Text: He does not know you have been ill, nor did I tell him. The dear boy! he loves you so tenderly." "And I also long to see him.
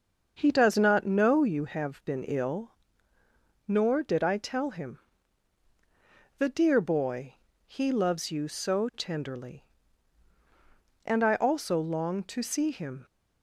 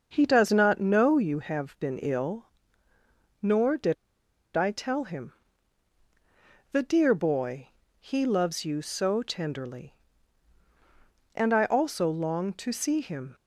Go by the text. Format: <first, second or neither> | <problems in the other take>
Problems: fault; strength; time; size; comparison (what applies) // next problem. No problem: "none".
first | starts louder than the rest; until 1.1 s; 6.5 dB; also in the first // pauses between "did" and "I"; noticeable; at 3.9 s; 0.60 s long